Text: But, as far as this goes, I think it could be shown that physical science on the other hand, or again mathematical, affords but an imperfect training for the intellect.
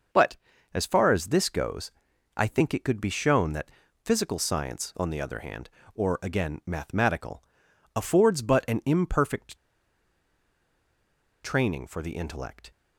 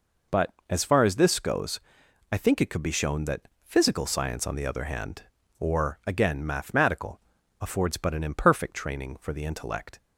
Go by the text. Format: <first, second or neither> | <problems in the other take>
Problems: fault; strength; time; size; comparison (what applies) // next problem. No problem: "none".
second | pauses between "that" and "physical"; slight; at 3.7 s; 0.32 s long // pauses between "imperfect" and "training"; strong; at 9.5 s; 1.8 s long